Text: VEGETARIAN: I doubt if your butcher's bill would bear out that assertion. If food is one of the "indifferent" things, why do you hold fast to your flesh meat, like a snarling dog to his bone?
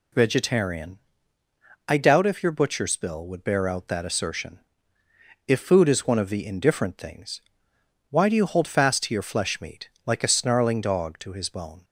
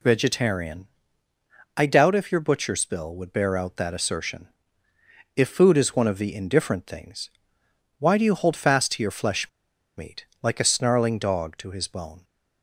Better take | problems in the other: first | pauses between "flesh" and "meat"; noticeable; at 9.4 s; 0.49 s long

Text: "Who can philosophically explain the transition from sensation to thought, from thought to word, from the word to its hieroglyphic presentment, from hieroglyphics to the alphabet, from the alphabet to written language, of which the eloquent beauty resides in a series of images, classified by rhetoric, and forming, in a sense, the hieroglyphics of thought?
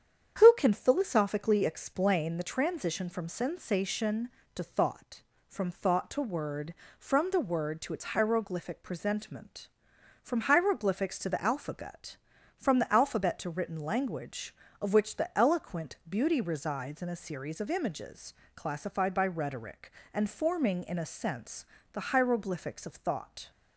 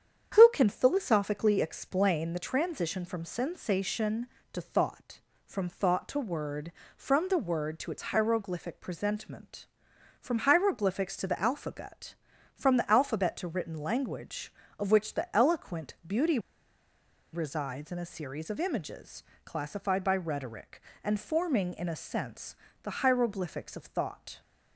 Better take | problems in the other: first | starts louder than the rest; strong; until 1.3 s; 8.5 dB; strong in the first // pauses between "beauty" and "resides"; noticeable; at 16.3 s; 0.94 s long

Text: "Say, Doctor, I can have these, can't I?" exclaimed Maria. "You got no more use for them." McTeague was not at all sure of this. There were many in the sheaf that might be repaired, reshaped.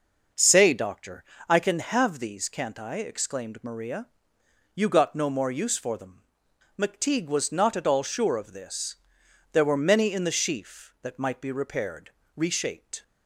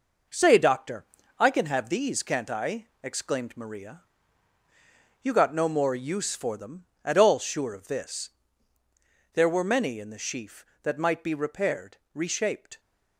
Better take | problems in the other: first | skips "McTeague was not"; at 6.9 s

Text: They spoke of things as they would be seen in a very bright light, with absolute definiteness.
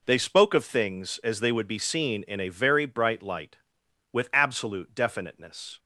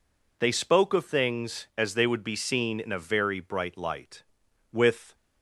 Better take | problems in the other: first | stops before "absolute definiteness"; at 5.1 s

